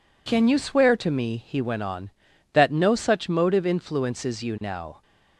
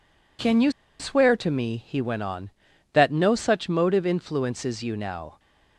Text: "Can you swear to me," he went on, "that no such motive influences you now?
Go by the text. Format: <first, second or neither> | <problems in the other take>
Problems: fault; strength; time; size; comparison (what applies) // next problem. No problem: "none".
first | pauses between "you" and "swear"; slight; at 0.6 s; 0.29 s long